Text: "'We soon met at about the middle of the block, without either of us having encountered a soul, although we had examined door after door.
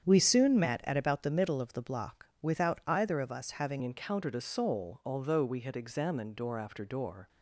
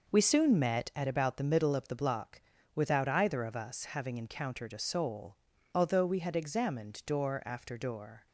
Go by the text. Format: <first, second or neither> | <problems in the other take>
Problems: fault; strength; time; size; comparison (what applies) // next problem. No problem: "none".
second | starts louder than the rest; strong; until 1.0 s; 8 dB // changes voice at "encountered"; from 3.8 s on; 3.4 s long